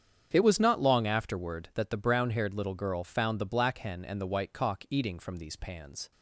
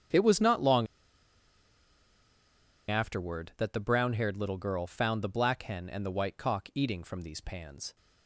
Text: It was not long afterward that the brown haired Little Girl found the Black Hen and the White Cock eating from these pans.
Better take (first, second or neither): first